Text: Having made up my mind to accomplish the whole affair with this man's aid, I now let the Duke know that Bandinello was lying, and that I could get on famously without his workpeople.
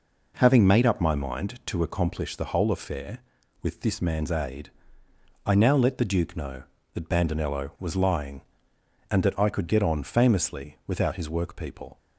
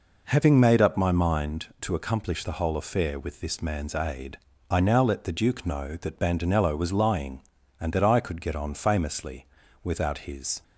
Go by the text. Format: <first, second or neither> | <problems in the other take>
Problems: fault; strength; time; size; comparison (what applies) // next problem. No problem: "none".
first | pauses between "famously" and "without"; at 9.4 s; 0.38 s long // stops before "workpeople"; at 10.6 s